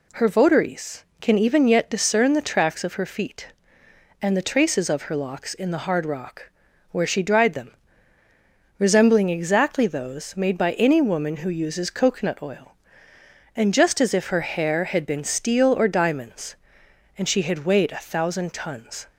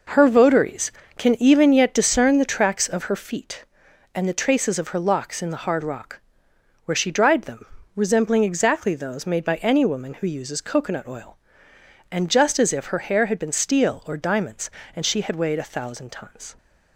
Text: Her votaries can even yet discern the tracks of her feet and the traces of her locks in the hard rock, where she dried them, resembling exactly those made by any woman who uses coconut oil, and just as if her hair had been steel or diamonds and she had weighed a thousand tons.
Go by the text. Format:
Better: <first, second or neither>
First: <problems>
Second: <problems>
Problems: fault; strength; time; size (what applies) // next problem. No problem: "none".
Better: neither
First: none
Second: none